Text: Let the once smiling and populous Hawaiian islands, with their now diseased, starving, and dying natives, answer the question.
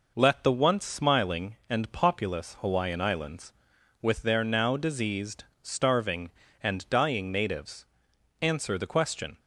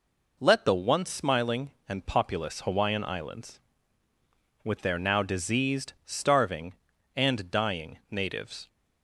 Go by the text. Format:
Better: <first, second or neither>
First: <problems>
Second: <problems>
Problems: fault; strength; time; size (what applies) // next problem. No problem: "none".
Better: first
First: none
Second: stops before "answer the question"; at 8.6 s